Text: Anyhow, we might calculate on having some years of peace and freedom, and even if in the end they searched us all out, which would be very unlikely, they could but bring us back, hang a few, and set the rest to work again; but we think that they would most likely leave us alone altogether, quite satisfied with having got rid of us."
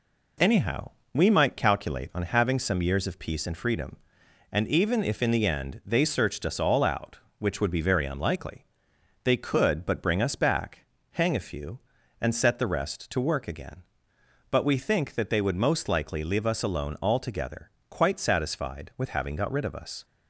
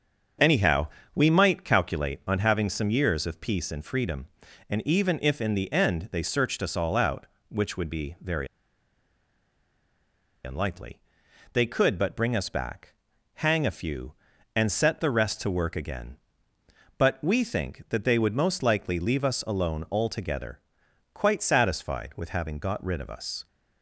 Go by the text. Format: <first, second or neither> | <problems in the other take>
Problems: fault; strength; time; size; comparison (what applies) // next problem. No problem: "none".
first | starts louder than the rest; until 1.6 s; 6.5 dB // pauses between "very" and "unlikely"; strong; at 8.4 s; 1.9 s long